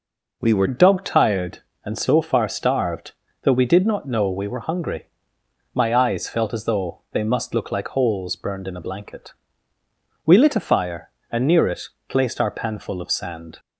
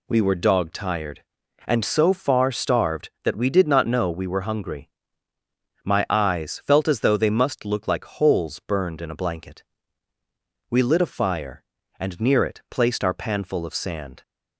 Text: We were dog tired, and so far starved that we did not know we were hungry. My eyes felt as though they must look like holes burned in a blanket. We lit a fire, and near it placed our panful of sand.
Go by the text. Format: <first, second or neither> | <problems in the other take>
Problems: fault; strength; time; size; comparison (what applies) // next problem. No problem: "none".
second | changes voice at "dog"; from 0.6 s on; 12.9 s long // pauses between "it" and "placed"; slight; at 11.8 s; 0.22 s long